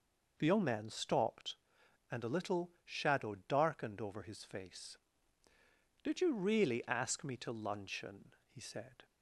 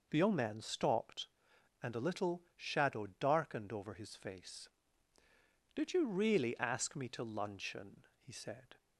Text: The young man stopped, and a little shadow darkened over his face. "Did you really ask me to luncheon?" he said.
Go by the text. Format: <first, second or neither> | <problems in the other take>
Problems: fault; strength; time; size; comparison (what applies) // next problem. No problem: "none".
neither | none